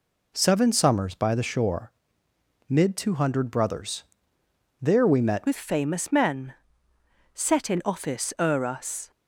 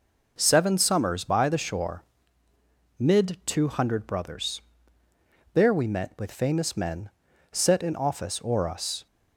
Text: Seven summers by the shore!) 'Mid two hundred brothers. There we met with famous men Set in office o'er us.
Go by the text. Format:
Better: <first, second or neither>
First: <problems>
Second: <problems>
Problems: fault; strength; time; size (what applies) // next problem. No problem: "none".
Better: second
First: changes voice at "with"; from 5.4 s on; 3.7 s long // pauses between "men" and "Set"; noticeable; at 6.5 s; 0.80 s long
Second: pauses between "men" and "Set"; at 7.0 s; 0.42 s long